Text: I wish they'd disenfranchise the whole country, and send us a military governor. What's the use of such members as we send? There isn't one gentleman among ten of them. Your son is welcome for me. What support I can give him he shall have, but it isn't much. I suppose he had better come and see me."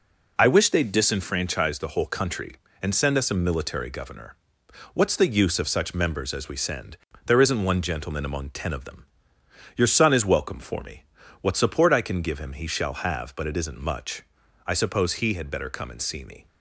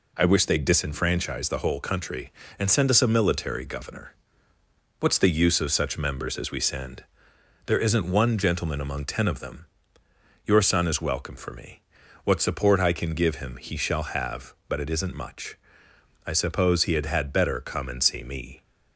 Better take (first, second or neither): first